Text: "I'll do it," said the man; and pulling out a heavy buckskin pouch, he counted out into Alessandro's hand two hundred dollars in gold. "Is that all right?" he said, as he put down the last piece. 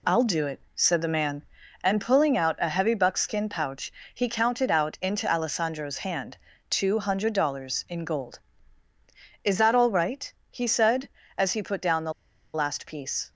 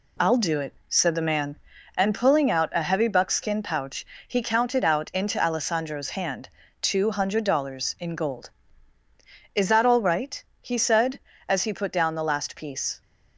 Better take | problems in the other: second | pauses between "hand" and "two"; slight; at 6.3 s; 0.32 s long; slight in the second // pauses between "the" and "last"; at 12.1 s; 0.41 s long

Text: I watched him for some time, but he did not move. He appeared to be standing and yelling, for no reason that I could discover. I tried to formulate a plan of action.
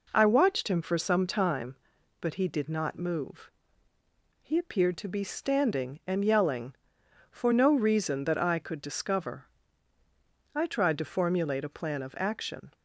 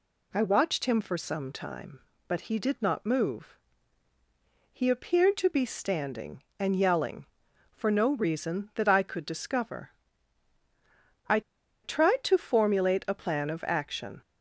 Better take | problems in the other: first | pauses between "I" and "tried"; at 11.3 s; 0.44 s long

